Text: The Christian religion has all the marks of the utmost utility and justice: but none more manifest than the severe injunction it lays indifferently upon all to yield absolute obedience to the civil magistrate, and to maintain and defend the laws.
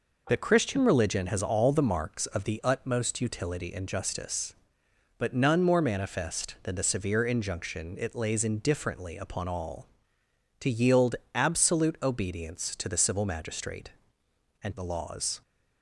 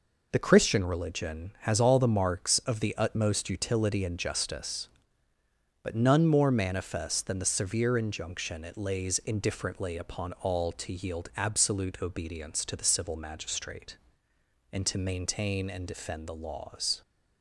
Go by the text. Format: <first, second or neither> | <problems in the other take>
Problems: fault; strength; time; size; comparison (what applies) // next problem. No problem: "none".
second | pauses between "yield" and "absolute"; slight; at 11.1 s; 0.20 s long // skips "to maintain and defend"; at 14.7 s